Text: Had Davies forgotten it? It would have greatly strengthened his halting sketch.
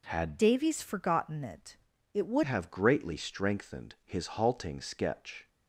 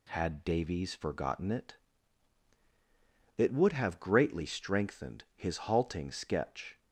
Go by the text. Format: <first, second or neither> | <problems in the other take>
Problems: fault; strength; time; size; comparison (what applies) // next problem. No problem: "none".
second | changes voice from "Davies" to "would"; from 0.3 to 2.4 s; 2.1 s long